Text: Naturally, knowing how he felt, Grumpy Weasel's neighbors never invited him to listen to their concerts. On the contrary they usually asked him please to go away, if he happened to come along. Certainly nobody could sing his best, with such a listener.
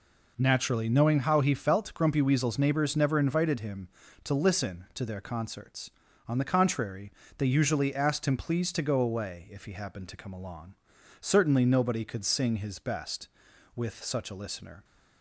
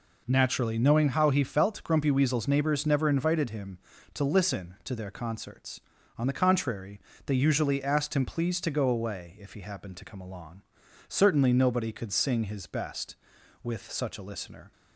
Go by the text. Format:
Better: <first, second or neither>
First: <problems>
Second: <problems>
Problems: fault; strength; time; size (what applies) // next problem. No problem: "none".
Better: neither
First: pauses between "contrary" and "they"; slight; at 7.1 s; 0.26 s long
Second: pauses between "contrary" and "they"; slight; at 7.0 s; 0.26 s long